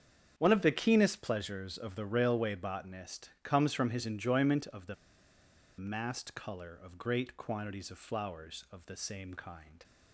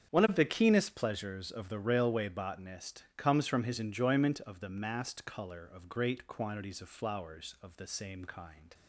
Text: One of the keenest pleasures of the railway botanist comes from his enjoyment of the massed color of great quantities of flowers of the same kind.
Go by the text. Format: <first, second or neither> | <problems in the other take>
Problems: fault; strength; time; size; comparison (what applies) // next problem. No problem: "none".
second | starts louder than the rest; strong; until 1.3 s; 7.5 dB; strong in the second // pauses between "the" and "massed"; noticeable; at 4.9 s; 0.84 s long